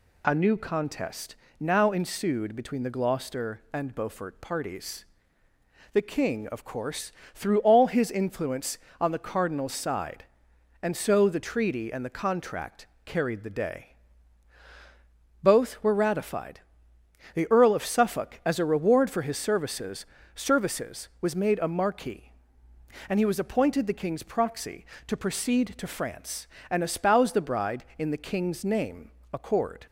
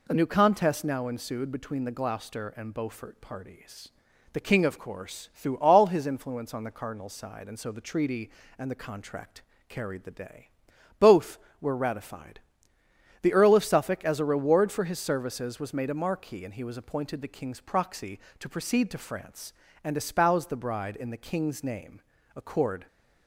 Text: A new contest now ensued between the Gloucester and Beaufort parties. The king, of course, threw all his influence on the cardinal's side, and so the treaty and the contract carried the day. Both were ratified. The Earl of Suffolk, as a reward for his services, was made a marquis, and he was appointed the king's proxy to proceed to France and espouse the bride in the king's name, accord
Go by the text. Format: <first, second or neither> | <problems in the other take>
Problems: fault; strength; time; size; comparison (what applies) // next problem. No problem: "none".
second | pauses between "contest" and "now"; slight; at 1.3 s; 0.24 s long // pauses between "contract" and "carried"; slight; at 12.8 s; 0.18 s long; slight in the second // says "services" twice; at 20.3 s